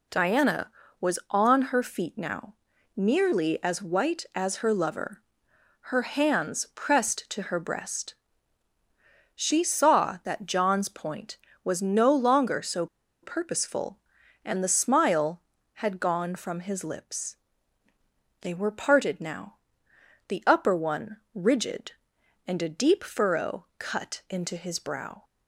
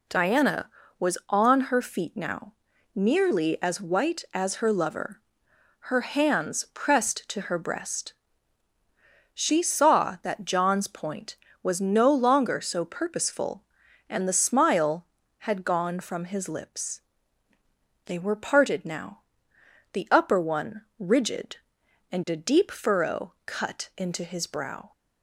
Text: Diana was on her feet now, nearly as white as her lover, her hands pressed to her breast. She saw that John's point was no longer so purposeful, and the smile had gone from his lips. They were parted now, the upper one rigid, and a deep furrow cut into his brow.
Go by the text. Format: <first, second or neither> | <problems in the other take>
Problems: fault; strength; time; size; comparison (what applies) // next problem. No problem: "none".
second | pauses between "so" and "purposeful"; at 12.8 s; 0.36 s long